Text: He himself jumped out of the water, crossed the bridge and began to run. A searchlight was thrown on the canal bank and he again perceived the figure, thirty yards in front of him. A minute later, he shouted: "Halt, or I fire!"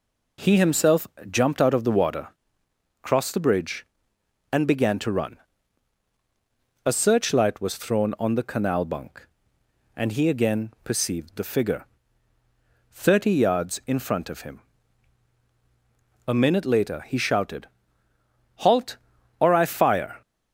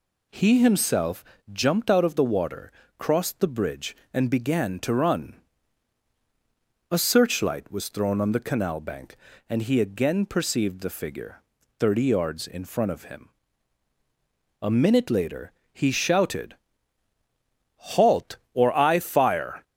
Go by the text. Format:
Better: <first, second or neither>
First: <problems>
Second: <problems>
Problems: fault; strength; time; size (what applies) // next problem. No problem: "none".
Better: second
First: pauses between "himself" and "jumped"; slight; at 1.0 s; 0.24 s long // says "bunk" for "bank"; at 8.8 s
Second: pauses between "himself" and "jumped"; slight; at 1.2 s; 0.26 s long